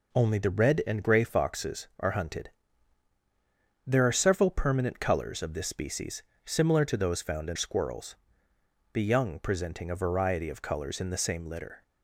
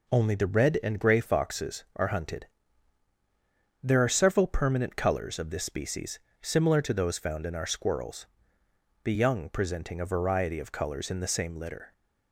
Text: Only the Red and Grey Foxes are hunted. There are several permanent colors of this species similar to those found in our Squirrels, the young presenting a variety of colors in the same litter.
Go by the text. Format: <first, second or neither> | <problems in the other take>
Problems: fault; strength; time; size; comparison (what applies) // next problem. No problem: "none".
second | pauses between "species" and "similar"; slight; at 6.2 s; 0.20 s long; slight in the second // skips "our"; at 7.5 s